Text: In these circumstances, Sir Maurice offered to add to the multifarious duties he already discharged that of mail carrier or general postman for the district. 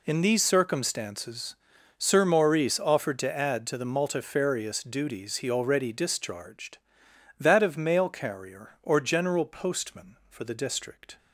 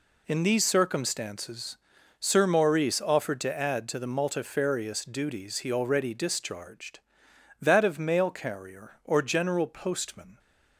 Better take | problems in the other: first | stops before "for the district"; at 10.3 s

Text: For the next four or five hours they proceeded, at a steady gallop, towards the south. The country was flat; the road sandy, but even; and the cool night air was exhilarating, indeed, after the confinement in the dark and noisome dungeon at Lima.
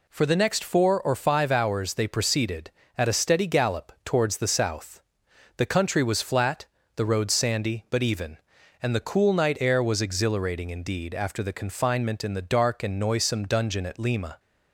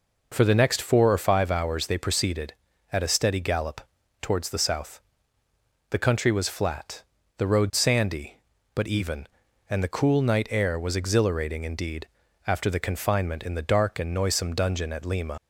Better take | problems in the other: first | leaves "Lima" unfinished; at 15.3 s; 95 ms

